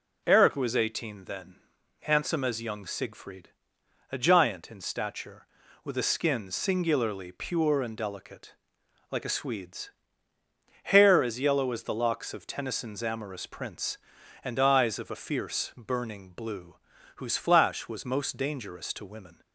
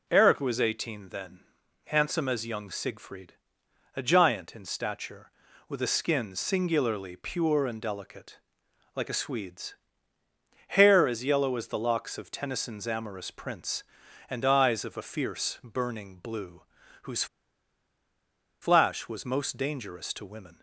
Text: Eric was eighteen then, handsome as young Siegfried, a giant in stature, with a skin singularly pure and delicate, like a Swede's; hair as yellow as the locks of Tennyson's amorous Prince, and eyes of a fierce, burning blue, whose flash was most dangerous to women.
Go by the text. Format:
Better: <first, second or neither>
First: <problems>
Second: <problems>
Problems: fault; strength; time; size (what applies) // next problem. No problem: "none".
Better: first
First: none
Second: pauses between "whose" and "flash"; strong; at 17.2 s; 1.3 s long